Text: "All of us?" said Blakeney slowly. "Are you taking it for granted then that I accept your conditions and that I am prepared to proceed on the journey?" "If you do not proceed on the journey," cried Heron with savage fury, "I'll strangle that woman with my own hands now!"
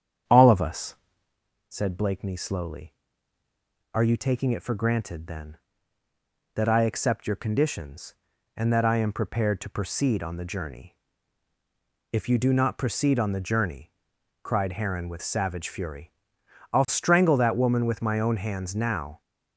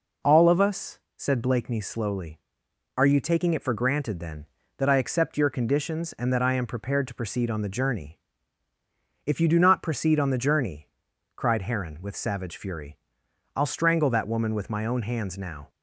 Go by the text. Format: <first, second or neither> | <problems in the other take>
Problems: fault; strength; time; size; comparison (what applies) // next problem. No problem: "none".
second | starts louder than the rest; strong; until 1.4 s; 8.5 dB